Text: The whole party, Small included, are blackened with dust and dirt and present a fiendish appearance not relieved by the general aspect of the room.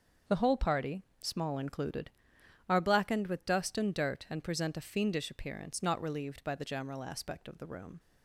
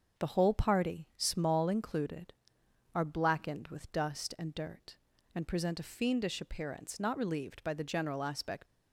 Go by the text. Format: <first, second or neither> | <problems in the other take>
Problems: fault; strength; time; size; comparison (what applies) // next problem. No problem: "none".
first | starts louder than the rest; until 1.2 s; 6.5 dB; also in the first // stops before "of the room"; at 8.6 s